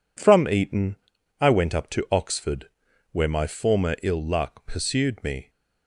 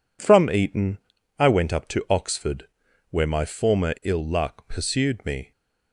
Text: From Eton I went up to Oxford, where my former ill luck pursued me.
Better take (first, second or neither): neither